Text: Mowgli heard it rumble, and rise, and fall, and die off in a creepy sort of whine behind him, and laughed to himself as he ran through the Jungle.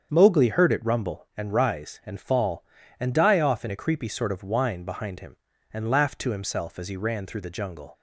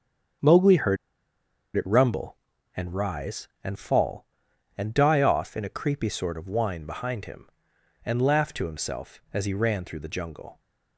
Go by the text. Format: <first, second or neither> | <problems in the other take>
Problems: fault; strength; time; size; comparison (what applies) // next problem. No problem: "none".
first | starts louder than the rest; strong; until 2.2 s; 7.5 dB; strong in the first // pauses between "heard" and "it"; noticeable; at 0.9 s; 0.80 s long